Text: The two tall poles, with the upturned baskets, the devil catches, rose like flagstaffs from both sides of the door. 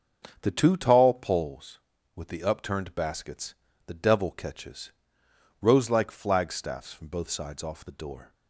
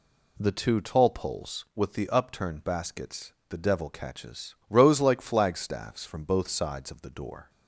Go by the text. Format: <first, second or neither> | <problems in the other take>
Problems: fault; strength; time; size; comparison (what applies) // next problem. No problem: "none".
second | starts louder than the rest; until 1.4 s; 7 dB // says "off" for "of"; at 7.6 s